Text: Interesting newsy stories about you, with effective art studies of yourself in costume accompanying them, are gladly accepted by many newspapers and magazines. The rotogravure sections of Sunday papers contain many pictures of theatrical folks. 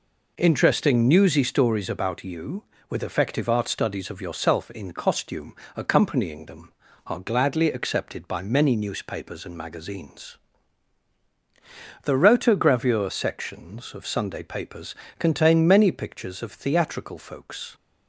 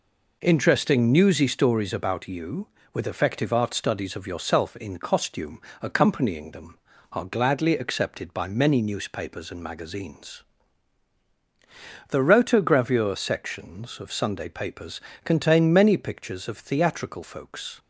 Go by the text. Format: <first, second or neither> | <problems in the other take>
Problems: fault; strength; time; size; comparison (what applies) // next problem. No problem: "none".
neither | pauses between "costume" and "accompanying"; slight; the same in both // pauses between "papers" and "contain"; slight; the same in both